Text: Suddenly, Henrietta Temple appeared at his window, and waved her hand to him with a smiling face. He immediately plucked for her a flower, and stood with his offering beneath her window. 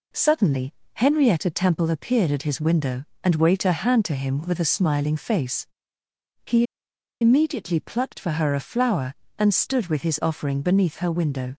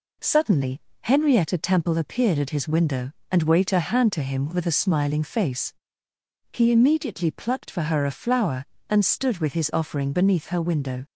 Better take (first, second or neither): second